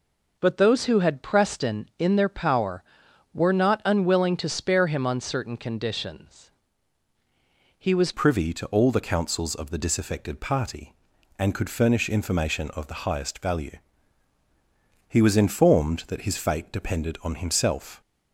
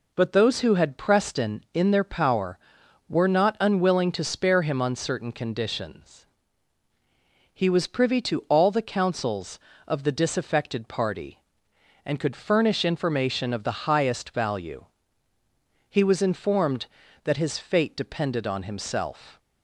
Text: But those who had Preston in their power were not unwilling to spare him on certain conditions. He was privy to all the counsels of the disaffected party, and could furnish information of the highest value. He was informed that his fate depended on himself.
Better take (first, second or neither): second